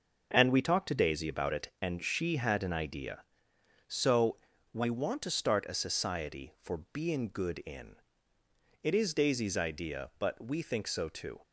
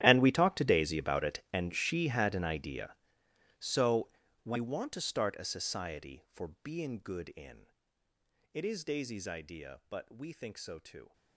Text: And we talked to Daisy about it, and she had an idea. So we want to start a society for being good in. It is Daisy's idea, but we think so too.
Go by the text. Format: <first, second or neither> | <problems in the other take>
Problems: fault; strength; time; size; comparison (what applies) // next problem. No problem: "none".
first | gets quieter; strong; throughout; 18 dB // pauses between "So" and "we"; slight; at 4.0 s; 0.36 s long; slight in the first